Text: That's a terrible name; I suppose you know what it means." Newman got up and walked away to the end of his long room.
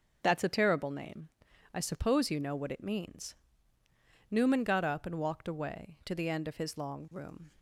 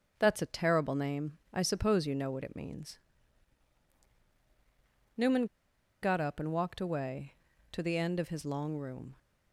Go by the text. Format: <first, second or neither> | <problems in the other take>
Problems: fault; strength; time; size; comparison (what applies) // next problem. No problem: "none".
first | starts louder than the rest; until 1.1 s; 6.5 dB; noticeable in the first // pauses between "Newman" and "got"; noticeable; at 5.4 s; 0.56 s long